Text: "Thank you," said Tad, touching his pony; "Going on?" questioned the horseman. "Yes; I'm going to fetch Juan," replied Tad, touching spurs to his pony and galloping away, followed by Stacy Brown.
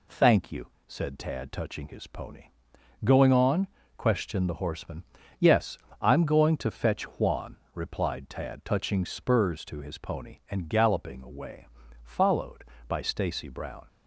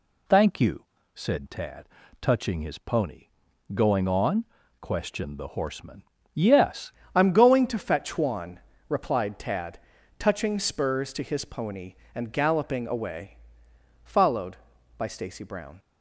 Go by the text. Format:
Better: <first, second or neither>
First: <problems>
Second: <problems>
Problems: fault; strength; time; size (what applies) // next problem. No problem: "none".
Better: first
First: none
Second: changes voice at "I'm"; from 7.1 s on; 8.6 s long